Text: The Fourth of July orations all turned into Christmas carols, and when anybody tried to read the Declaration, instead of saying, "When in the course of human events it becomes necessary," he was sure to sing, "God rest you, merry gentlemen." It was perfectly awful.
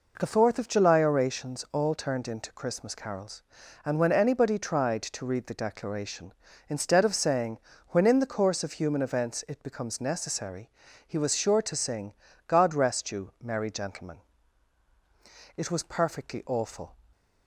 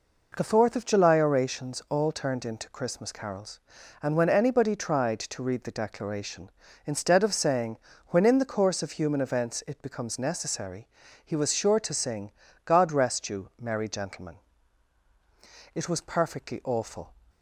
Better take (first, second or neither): neither